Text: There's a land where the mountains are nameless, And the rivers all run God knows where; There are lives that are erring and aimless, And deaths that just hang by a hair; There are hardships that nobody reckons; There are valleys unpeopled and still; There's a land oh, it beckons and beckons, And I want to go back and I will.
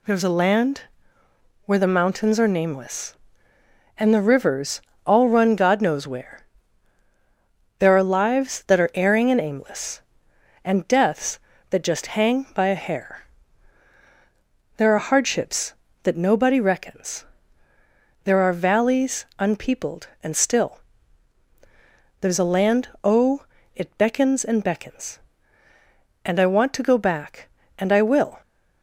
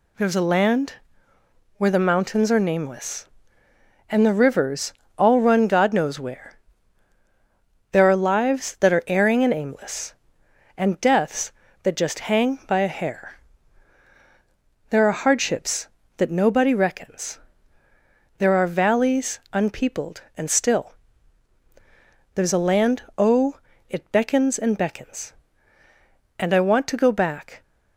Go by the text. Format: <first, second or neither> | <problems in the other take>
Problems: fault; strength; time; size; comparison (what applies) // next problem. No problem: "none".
first | pauses between "land" and "where"; noticeable; at 0.9 s; 0.84 s long; noticeable in the first // pauses between "rivers" and "all"; slight; at 4.9 s; 0.26 s long; slight in the first // pauses between "land" and "oh"; slight; at 23.0 s; 0.16 s long; slight in the first // stops before "and I will"; at 27.6 s